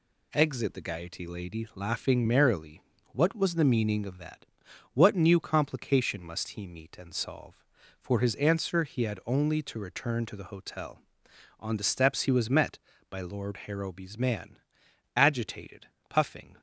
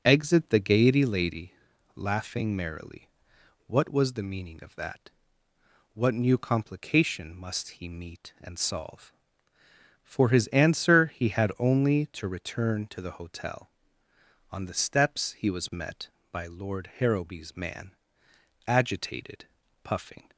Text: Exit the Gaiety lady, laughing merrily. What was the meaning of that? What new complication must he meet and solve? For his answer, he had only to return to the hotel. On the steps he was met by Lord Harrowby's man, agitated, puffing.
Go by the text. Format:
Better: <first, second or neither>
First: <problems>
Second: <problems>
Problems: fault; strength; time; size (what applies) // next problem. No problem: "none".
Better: neither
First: none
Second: none